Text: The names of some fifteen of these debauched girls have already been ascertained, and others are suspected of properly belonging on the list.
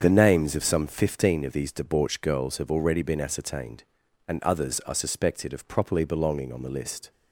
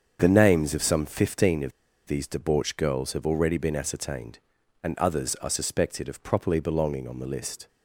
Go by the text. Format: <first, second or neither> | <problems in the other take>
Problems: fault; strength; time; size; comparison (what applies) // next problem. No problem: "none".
first | starts louder than the rest; until 1.2 s; 7 dB; also in the first // pauses between "of" and "these"; slight; at 1.7 s; 0.35 s long